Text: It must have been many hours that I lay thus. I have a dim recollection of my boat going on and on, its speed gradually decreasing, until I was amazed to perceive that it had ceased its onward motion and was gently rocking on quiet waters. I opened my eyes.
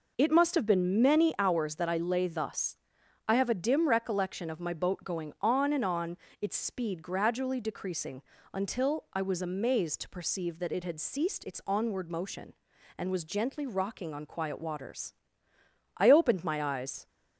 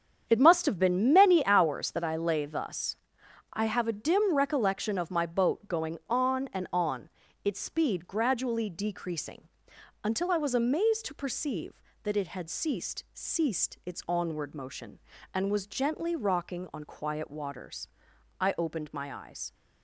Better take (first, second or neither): first